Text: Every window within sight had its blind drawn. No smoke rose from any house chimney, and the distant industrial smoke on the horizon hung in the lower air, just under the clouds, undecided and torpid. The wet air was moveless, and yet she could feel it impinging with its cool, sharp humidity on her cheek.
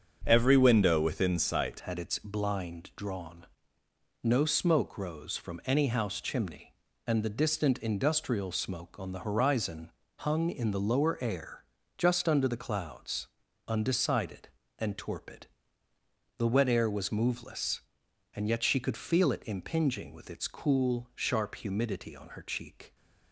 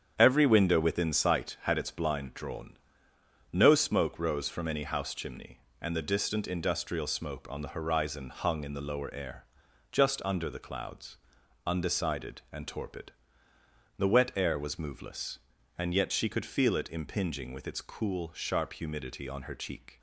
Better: second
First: starts louder than the rest; until 1.2 s; 7 dB // changes voice at "had"; from 1.8 s on; 21.1 s long // pauses between "horizon" and "hung"; slight; at 9.9 s; 0.30 s long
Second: starts louder than the rest; strong; until 1.1 s; 8 dB

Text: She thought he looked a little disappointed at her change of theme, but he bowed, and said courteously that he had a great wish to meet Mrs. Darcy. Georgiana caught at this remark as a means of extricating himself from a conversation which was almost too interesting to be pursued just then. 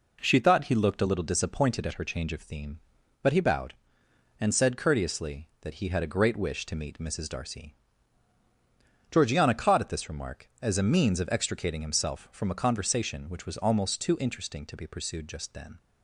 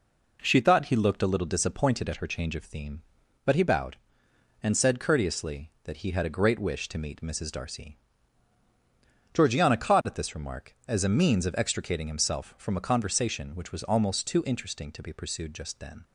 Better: neither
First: none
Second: none

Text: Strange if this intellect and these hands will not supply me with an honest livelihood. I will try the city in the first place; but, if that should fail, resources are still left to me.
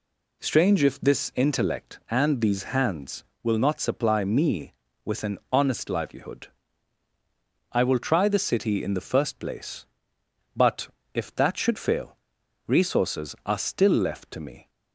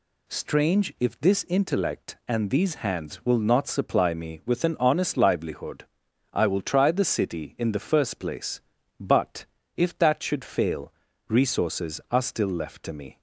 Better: neither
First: none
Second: none

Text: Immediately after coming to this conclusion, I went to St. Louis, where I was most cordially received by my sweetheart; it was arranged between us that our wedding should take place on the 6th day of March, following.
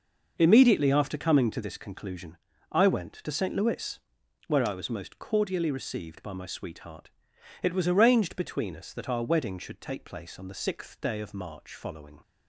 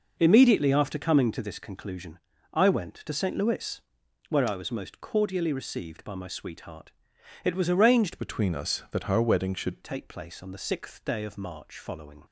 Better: first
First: none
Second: changes voice from "between" to "should"; from 8.1 to 9.8 s; 1.7 s long

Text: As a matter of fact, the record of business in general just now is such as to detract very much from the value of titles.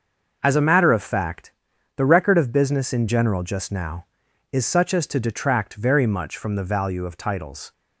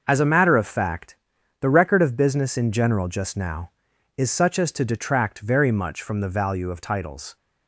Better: neither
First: starts louder than the rest; noticeable; until 1.4 s; 6 dB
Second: starts louder than the rest; noticeable; until 1.0 s; 6 dB

